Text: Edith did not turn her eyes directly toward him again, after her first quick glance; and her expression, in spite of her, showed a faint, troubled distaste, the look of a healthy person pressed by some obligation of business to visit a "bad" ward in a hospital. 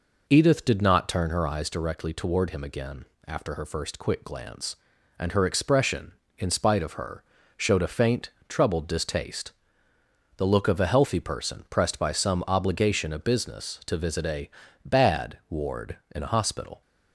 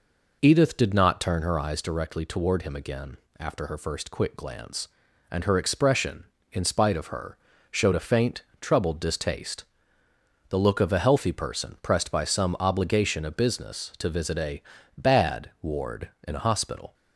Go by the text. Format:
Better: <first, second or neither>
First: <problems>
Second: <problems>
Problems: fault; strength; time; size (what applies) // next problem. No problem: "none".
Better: neither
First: pauses between "a" and "bad"; slight; at 14.4 s; 0.34 s long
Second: pauses between "a" and "bad"; slight; at 14.6 s; 0.34 s long